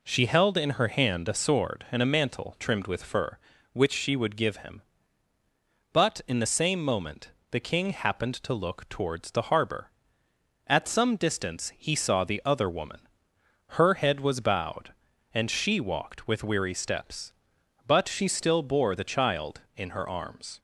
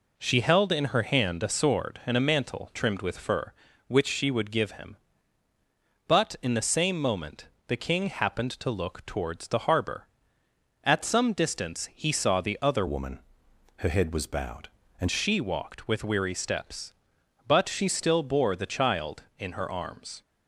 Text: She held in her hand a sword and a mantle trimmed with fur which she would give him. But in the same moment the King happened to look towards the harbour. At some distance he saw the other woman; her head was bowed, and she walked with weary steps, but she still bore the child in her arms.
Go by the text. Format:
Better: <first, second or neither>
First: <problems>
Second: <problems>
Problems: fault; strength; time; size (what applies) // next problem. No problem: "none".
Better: first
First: pauses between "moment" and "the"; slight; at 7.3 s; 0.20 s long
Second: pauses between "moment" and "the"; slight; at 7.4 s; 0.20 s long // changes voice from "woman" to "and"; from 12.8 to 15.0 s; 2.2 s long